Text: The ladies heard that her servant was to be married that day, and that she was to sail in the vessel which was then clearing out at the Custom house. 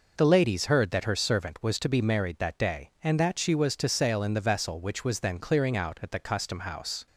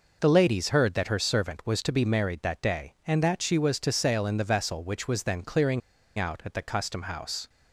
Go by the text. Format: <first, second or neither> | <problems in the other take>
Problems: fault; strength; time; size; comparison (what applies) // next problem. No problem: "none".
first | pauses between "clearing" and "out"; at 5.8 s; 0.36 s long